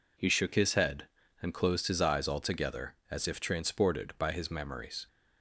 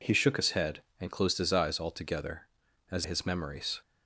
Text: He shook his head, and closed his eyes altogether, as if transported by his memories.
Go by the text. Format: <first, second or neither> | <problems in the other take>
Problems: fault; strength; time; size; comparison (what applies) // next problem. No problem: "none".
first | skips "if transported by"; at 3.0 s